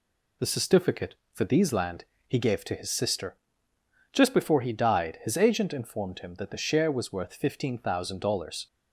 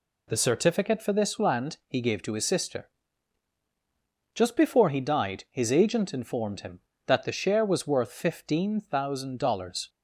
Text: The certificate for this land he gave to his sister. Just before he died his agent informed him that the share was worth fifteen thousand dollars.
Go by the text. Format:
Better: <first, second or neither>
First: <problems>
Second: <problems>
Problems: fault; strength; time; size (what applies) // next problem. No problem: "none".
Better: second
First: says "these" for "this"; at 1.4 s // pauses between "land" and "he"; slight; at 2.0 s; 0.24 s long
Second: none